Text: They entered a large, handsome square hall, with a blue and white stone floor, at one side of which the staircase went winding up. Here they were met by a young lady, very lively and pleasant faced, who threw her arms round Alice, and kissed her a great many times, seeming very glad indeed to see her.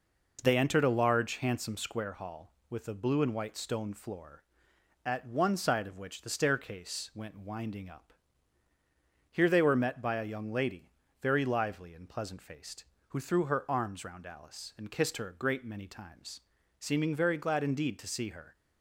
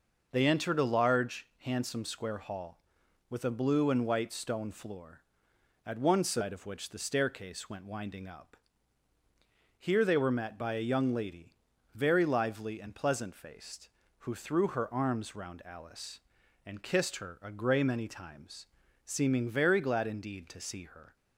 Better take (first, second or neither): first